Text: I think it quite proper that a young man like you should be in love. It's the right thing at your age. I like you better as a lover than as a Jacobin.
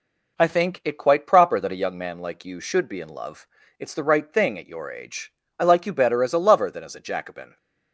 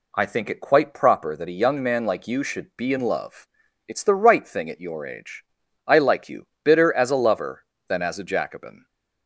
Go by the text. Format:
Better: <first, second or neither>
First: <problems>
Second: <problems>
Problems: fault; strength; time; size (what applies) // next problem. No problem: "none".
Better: first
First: none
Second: says "bitter" for "better"; at 6.6 s